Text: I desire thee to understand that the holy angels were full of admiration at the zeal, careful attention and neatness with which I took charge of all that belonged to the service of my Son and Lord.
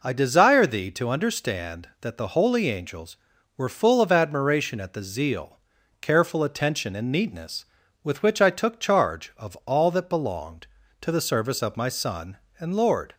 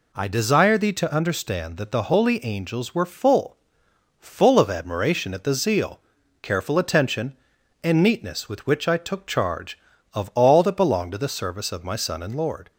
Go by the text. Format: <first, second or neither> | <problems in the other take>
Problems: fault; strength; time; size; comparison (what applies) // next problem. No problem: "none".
first | says "full" twice; at 4.1 s